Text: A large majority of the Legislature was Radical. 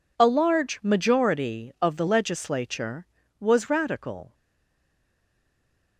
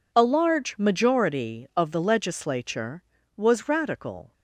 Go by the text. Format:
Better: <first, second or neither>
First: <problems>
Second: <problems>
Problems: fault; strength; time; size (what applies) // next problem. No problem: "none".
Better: second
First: stays silent after the last word; noticeable; from 4.3 s on; 1.6 s long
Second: none